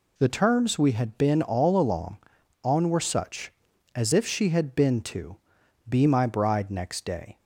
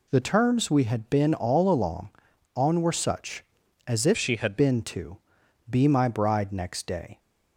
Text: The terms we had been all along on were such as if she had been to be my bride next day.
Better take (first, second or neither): first